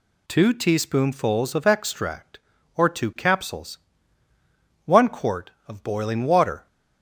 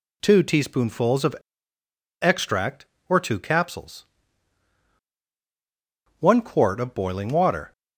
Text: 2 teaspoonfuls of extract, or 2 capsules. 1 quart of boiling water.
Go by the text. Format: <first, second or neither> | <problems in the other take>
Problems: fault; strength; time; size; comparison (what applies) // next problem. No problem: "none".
first | pauses between "of" and "extract"; noticeable; at 1.3 s; 0.87 s long